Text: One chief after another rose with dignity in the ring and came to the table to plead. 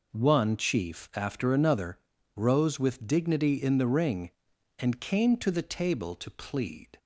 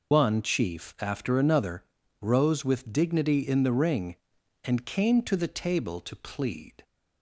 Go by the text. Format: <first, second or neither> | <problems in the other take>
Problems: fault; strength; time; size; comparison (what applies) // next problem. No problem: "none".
first | loses the start of "One"; at 0.1 s; 135 ms // pauses between "another" and "rose"; slight; at 1.8 s; 0.36 s long; slight in the first